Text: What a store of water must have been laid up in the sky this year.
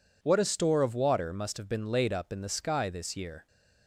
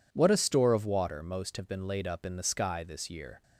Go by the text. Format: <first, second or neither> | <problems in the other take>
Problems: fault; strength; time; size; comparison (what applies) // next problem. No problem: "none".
first | says "most" for "must"; at 1.2 s